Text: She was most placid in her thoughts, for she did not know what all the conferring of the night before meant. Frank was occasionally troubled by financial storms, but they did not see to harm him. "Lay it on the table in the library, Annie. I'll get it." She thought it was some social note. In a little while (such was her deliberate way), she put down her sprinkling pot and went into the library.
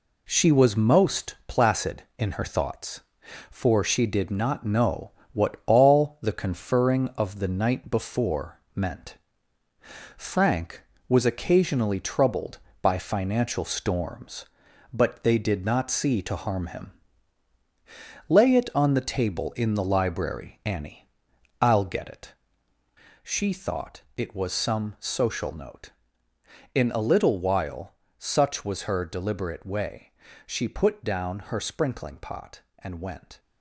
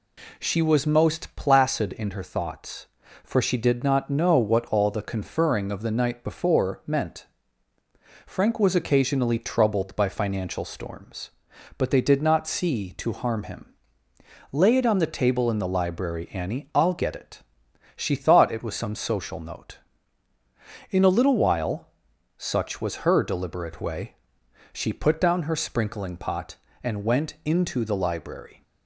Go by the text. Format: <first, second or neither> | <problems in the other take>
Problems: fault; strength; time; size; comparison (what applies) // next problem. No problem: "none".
second | pauses between "know" and "what"; slight; at 5.1 s; 0.20 s long // pauses between "before" and "meant"; slight; at 8.5 s; 0.16 s long // pauses between "thought" and "it"; slight; at 24.0 s; 0.16 s long // stops before "into the library"; at 33.3 s